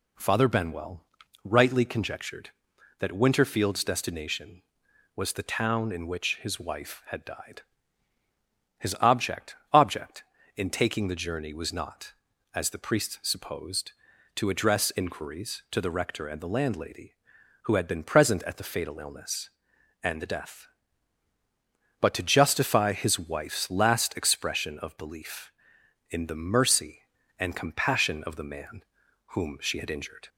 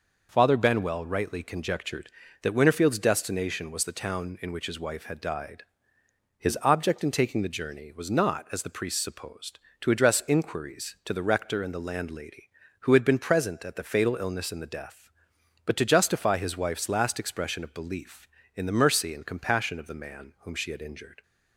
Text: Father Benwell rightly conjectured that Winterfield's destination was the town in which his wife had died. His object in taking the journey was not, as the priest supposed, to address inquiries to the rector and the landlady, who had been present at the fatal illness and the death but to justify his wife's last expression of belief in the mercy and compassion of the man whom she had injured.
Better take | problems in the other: second | pauses between "Benwell" and "rightly"; at 1.0 s; 0.40 s long // says "object" twice; at 9.7 s // pauses between "man" and "whom"; noticeable; at 28.8 s; 0.46 s long

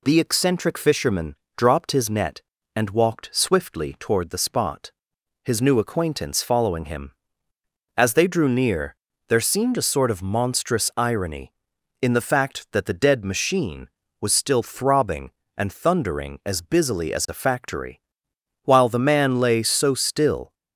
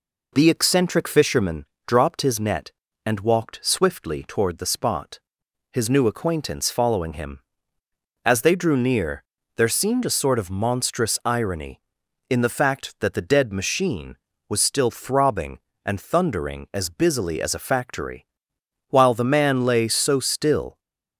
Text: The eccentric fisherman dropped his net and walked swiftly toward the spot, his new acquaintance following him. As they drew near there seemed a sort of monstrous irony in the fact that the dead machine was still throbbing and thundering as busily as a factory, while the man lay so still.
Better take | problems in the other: first | starts louder than the rest; until 1.5 s; 4 dB // pauses between "fisherman" and "dropped"; slight; at 1.6 s; 0.20 s long; slight in the first // pauses between "near" and "there"; slight; at 9.2 s; 0.34 s long; slight in the first

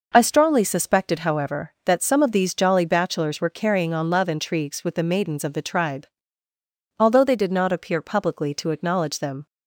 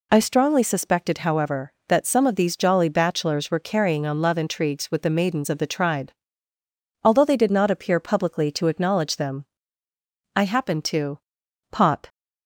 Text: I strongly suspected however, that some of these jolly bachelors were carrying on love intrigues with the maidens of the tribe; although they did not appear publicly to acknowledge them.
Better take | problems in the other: first | goes on to say "I happened to pop"; strong; from 10.3 s on; 1.7 s long

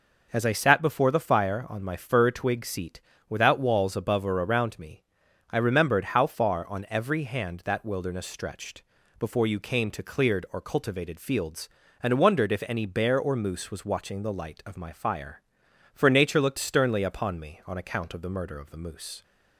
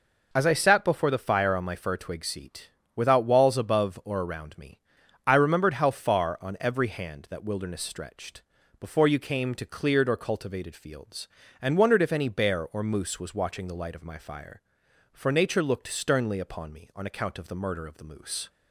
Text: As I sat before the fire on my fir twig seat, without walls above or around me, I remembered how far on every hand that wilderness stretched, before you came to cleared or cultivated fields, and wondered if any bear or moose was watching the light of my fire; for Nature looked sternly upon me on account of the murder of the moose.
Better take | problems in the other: neither | none

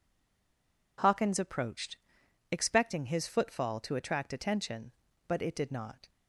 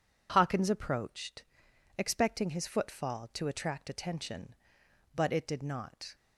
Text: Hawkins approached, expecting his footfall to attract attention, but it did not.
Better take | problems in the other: second | stays silent before the first word; slight; until 0.9 s; 0.9 s long

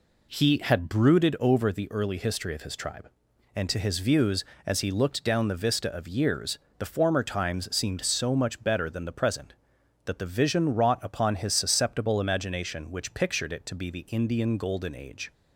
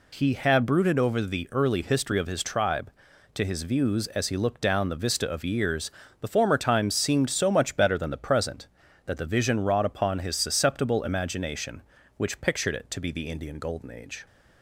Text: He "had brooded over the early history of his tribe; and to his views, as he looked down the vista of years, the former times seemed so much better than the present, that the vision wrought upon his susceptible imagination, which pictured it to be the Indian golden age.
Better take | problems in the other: first | skips "and"; at 3.1 s

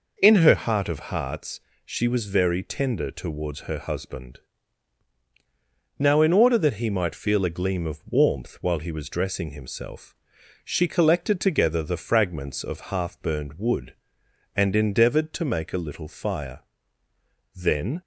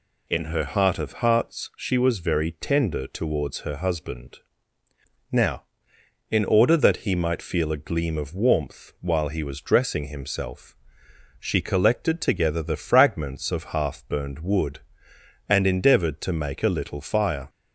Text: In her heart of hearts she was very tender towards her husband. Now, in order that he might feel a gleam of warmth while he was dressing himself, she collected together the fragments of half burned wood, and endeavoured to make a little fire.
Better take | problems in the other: second | pauses between "hearts" and "she"; slight; at 1.6 s; 0.24 s long // goes on to say "Then"; slight; from 17.5 s on; 0.46 s long

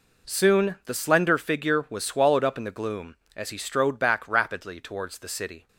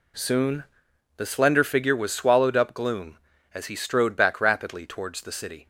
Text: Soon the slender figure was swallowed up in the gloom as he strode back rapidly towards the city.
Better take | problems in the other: first | pauses between "Soon" and "the"; noticeable; at 0.6 s; 0.54 s long // skips "in the"; at 2.7 s

